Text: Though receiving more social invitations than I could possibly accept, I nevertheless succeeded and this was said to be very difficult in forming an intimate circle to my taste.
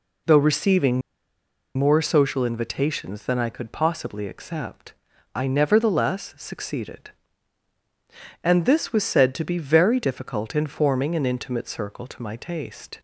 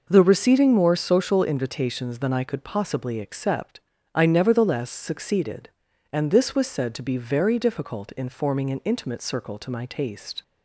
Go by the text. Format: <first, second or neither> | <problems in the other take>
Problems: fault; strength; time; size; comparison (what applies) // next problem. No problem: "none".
second | pauses between "receiving" and "more"; noticeable; at 1.0 s; 0.76 s long